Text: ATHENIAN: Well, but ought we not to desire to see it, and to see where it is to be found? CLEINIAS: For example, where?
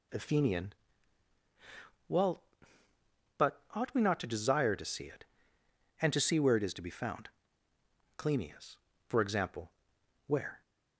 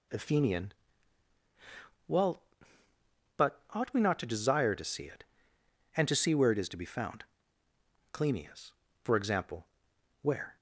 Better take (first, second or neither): neither